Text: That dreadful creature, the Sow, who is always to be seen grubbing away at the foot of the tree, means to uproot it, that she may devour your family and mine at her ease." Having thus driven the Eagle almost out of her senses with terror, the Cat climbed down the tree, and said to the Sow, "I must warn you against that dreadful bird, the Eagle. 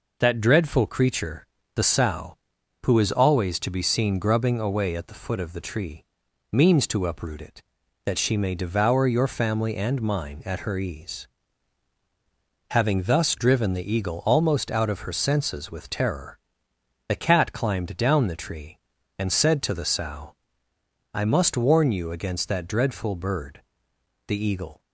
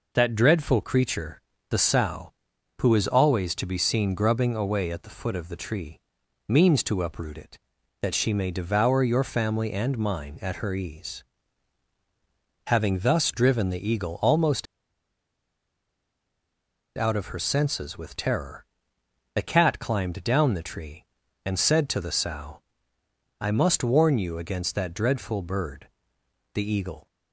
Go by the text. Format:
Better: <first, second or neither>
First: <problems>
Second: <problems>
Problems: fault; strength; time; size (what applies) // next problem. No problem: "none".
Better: first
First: none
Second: pauses between "almost" and "out"; strong; at 14.6 s; 2.3 s long